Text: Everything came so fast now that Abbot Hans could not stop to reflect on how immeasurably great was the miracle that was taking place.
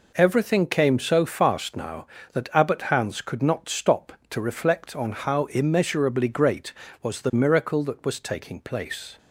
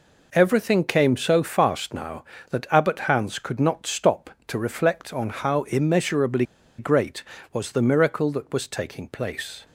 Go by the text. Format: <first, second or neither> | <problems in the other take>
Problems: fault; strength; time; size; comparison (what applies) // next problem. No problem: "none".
first | pauses between "immeasurably" and "great"; slight; at 6.4 s; 0.34 s long